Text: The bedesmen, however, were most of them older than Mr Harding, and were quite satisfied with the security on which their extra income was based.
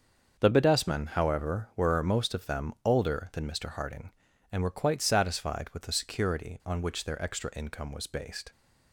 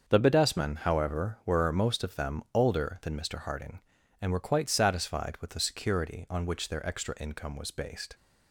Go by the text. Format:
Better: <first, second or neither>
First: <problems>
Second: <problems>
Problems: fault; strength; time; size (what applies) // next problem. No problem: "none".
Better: neither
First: starts louder than the rest; until 1.4 s; 6.5 dB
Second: starts louder than the rest; until 1.0 s; 6.5 dB